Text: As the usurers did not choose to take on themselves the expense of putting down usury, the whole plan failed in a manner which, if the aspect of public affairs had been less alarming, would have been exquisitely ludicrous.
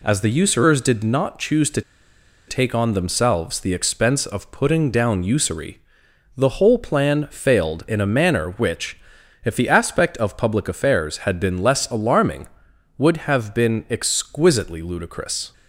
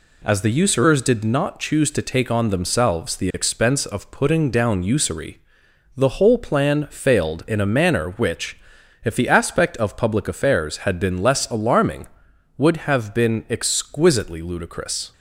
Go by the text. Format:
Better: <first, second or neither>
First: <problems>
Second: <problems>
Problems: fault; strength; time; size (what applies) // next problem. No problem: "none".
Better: second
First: pauses between "to" and "take"; noticeable; at 1.8 s; 0.67 s long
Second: none